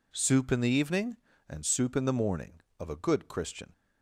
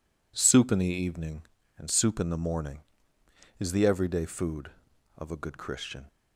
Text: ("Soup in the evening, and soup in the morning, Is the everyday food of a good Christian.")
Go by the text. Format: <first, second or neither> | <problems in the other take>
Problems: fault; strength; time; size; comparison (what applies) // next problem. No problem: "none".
second | skips "Is the everyday food"; at 2.6 s